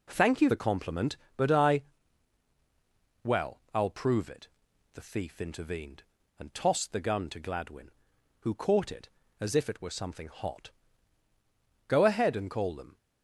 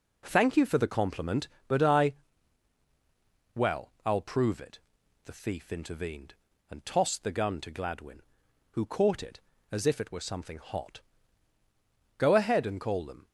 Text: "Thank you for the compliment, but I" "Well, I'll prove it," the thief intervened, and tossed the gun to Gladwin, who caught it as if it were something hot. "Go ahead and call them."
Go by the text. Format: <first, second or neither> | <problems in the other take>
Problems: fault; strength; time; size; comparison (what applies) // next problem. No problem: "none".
second | skips "for"; at 0.4 s // pauses between "I" and "Well"; strong; at 1.8 s; 1.4 s long; strong in the second